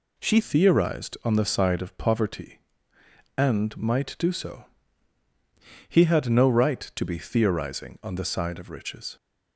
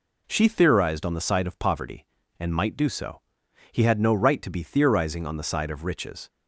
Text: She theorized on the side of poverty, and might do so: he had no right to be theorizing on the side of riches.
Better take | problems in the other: second | changes voice at "theorized"; from 0.4 s on; 8.7 s long

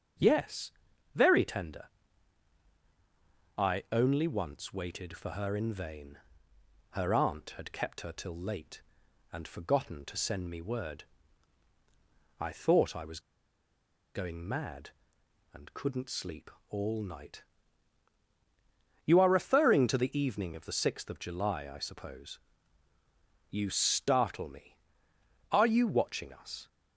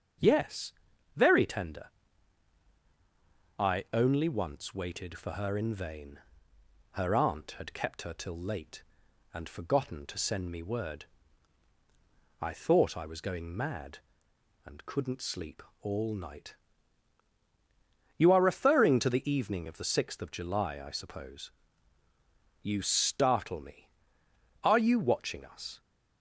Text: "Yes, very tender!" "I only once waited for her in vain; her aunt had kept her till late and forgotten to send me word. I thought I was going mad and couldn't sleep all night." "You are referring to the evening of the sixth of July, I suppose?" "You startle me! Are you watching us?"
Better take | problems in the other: second | starts louder than the rest; until 1.6 s; 7 dB; also in the second // pauses between "was" and "going"; noticeable; at 13.1 s; 0.94 s long // pauses between "sleep" and "all"; slight; at 16.4 s; 0.20 s long; slight in the second

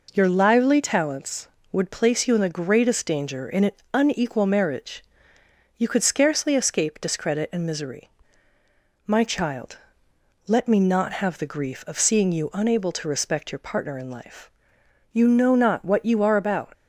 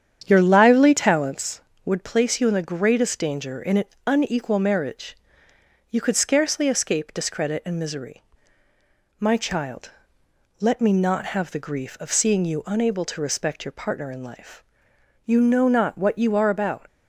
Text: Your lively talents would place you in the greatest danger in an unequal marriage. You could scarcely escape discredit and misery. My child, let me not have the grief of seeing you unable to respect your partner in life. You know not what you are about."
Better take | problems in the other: first | starts louder than the rest; strong; until 1.6 s; 8.5 dB // pauses between "an" and "unequal"; slight; at 3.8 s; 0.22 s long; slight in the first

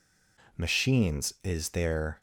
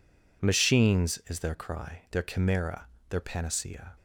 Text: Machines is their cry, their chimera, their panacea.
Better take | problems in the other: second | stops before "cry their chimera their panacea"; at 2.1 s

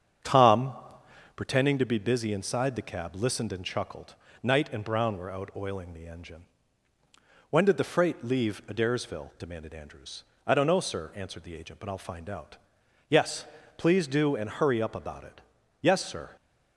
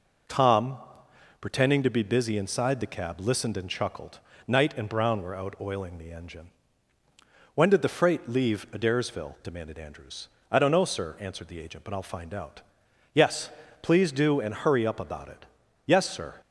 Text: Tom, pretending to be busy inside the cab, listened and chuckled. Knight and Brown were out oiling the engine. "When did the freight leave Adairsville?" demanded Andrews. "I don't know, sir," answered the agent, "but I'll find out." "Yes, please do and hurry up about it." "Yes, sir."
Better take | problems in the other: second | starts louder than the rest; strong; until 1.6 s; 8 dB

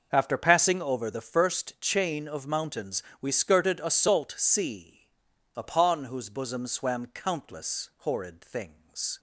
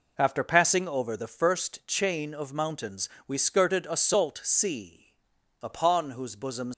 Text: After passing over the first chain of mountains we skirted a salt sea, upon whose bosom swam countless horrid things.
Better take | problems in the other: first | pauses between "mountains" and "we"; slight; at 3.0 s; 0.18 s long; slight in the first // stops before "swam countless horrid things"; at 6.7 s

